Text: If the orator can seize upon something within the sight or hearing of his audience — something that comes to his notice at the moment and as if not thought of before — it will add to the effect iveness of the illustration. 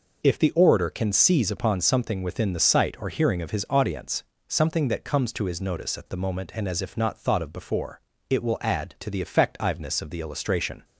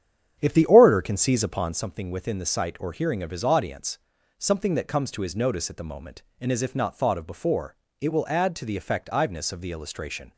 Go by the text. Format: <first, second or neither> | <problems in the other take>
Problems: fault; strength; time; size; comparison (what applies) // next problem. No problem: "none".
first | starts louder than the rest; strong; until 1.8 s; 8.5 dB